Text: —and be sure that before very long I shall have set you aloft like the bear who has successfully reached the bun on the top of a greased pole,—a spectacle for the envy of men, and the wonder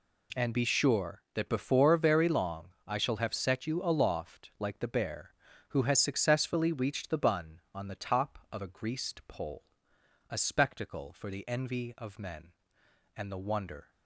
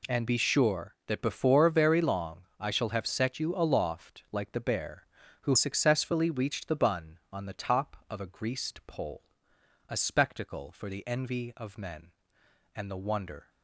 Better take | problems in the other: first | pauses between "long" and "I"; slight; at 2.4 s; 0.18 s long; slight in the first // skips "has"; at 5.5 s

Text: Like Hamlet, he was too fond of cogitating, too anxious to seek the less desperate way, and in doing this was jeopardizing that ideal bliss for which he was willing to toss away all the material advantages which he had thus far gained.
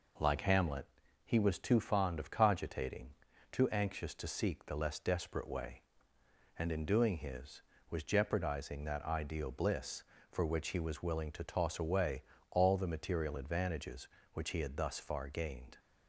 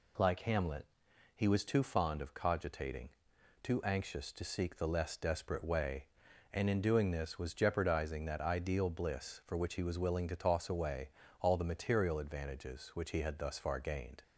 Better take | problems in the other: second | says "his" for "this"; at 7.1 s // pauses between "away" and "all"; slight; at 12.2 s; 0.28 s long; slight in the second

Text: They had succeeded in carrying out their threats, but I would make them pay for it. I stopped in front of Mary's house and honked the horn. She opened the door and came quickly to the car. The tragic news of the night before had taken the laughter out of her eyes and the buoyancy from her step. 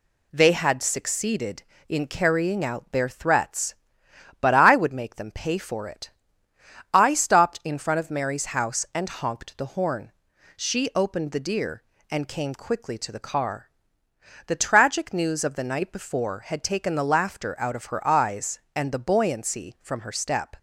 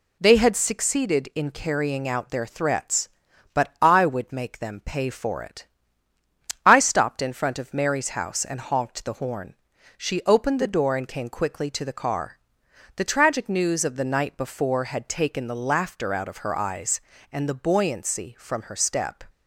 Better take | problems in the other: second | says "deer" for "door"; at 11.3 s

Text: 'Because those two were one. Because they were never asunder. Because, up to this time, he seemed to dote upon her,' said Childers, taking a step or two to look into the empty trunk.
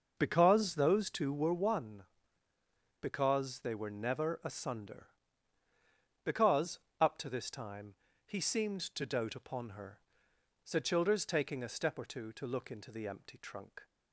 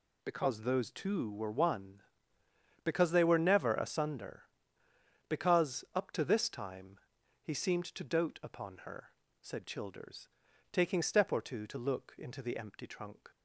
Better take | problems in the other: first | skips "a"; at 11.0 s

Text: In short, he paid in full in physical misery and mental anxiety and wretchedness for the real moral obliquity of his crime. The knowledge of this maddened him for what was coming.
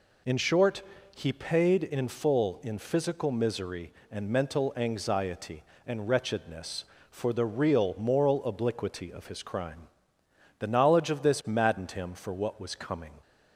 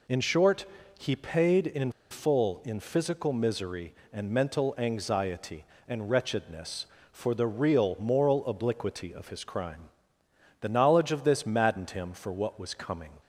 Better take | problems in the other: first | pauses between "in" and "full"; slight; at 1.9 s; 0.19 s long

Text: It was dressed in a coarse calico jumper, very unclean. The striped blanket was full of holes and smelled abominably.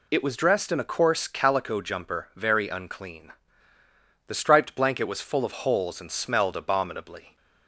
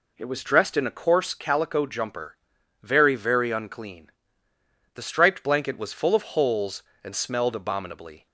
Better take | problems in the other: first | says "very" twice; at 3.1 s

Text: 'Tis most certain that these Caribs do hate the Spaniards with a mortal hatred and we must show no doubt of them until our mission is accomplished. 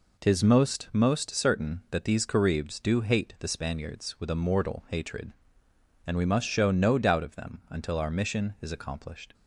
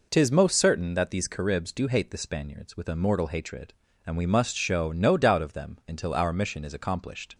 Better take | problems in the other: second | says "most" twice; at 0.9 s

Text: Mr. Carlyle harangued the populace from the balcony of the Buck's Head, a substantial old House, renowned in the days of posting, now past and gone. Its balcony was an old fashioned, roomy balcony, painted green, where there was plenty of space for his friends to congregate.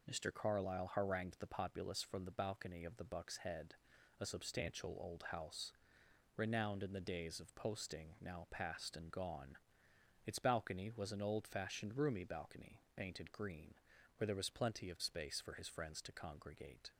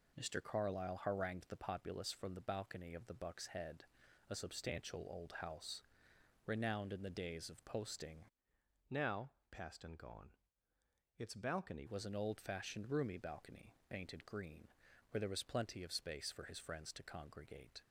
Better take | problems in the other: first | changes voice from "now" to "balcony"; from 8.8 to 11.8 s; 3.0 s long // pauses between "now" and "past"; slight; at 9.3 s; 0.18 s long

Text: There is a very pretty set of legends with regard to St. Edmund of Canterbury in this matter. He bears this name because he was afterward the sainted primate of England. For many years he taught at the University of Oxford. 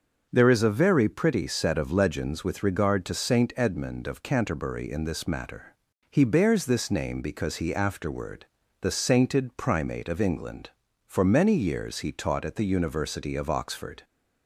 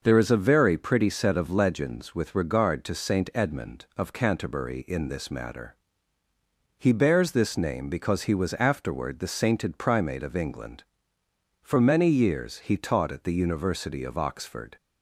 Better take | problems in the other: second | starts louder than the rest; until 1.3 s; 6.5 dB; noticeable in the second // skips "was"; at 7.7 s // pauses between "afterward" and "the"; at 8.4 s; 0.38 s long

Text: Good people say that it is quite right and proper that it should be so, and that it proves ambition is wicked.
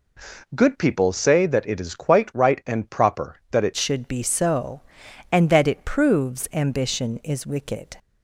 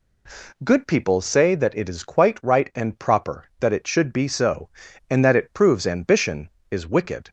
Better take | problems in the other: second | changes voice at "should"; from 3.7 s on; 4.2 s long

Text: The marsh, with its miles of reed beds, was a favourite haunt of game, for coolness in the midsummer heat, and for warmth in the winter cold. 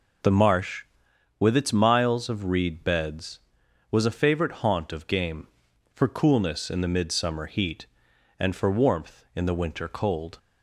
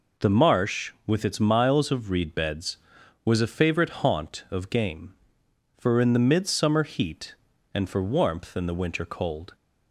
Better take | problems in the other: first | skips "coolness"; at 5.9 s

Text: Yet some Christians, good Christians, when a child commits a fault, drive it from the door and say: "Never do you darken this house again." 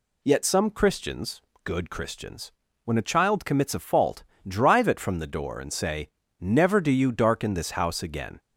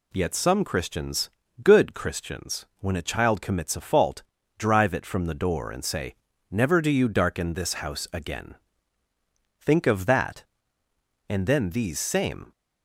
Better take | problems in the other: first | goes on to say "Think of that And then these same"; strong; from 9.6 s on; 2.9 s long

